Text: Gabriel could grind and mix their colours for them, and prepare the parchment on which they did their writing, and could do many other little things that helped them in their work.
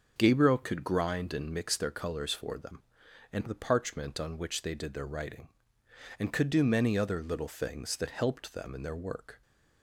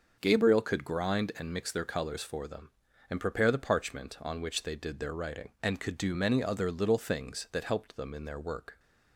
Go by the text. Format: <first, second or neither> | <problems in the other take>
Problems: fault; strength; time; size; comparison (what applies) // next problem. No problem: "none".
second | starts louder than the rest; noticeable; until 1.1 s; 6 dB; also in the second // skips "prepare"; at 3.4 s